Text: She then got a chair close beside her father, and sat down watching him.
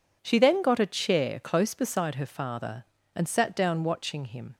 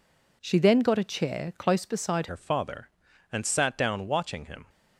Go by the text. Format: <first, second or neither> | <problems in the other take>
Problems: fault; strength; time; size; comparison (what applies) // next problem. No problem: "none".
first | changes voice at "her"; from 2.2 s on; 2.4 s long